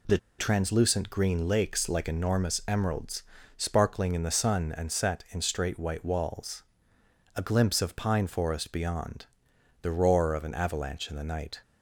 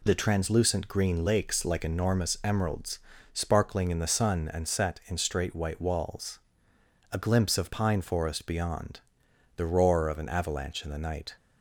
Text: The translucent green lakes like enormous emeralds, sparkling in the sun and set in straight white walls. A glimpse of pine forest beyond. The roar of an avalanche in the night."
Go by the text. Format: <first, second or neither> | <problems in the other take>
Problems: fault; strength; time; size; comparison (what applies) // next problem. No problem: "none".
second | pauses between "The" and "translucent"; slight; at 0.1 s; 0.20 s long